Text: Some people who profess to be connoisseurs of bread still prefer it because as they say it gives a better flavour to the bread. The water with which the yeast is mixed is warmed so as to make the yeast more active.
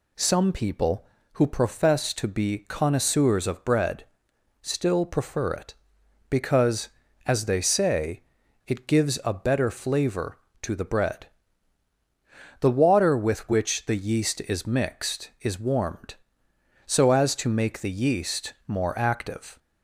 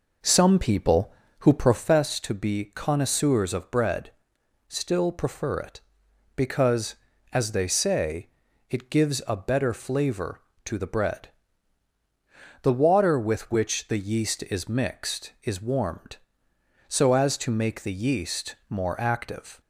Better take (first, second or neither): first